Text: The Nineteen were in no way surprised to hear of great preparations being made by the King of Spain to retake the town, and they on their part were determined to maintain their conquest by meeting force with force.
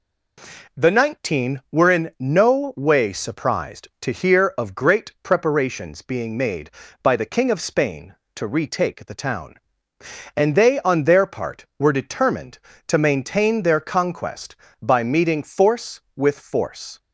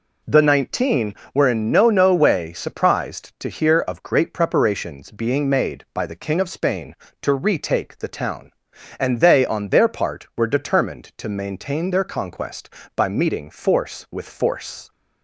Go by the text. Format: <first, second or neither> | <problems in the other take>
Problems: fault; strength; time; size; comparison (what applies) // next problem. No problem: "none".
first | says "no" twice; at 1.8 s